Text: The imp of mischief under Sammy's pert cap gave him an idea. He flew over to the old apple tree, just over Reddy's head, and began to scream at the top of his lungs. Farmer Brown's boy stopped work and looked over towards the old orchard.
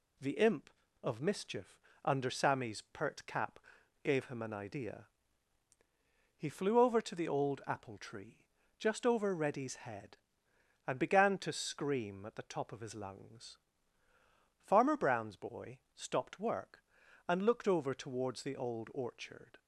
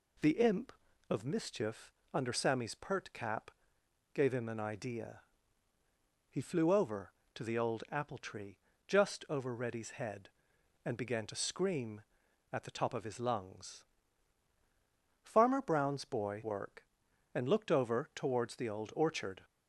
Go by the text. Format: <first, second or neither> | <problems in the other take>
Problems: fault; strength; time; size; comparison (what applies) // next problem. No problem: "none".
first | pauses between "mischief" and "under"; slight; at 1.9 s; 0.20 s long; slight in the first // pauses between "cap" and "gave"; noticeable; at 3.5 s; 0.62 s long; also in the first // skips "stopped"; at 16.4 s